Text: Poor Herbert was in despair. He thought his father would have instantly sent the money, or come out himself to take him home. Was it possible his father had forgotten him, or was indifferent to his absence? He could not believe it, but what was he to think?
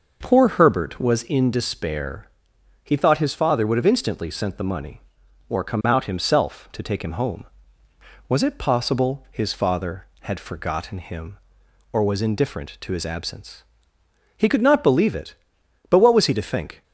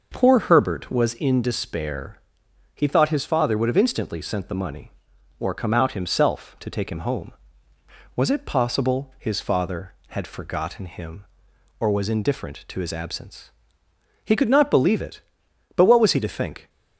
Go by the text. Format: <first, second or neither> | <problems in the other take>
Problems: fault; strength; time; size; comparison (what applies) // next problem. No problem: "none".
neither | none